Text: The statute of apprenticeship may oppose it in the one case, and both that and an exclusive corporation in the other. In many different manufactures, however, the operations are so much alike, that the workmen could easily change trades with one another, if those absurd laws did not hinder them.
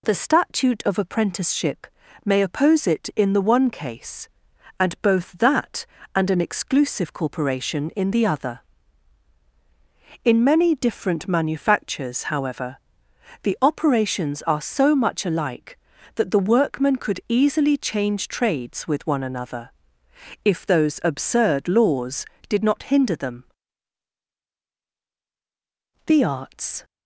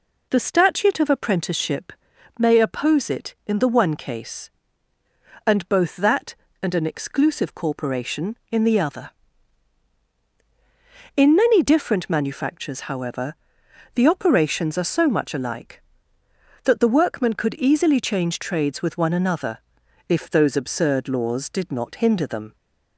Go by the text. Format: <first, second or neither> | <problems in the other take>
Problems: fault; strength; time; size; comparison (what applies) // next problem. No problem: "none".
second | pauses between "apprenticeship" and "may"; at 1.8 s; 0.40 s long; also in the second // goes on to say "The arts"; noticeable; from 26.0 s on; 0.80 s long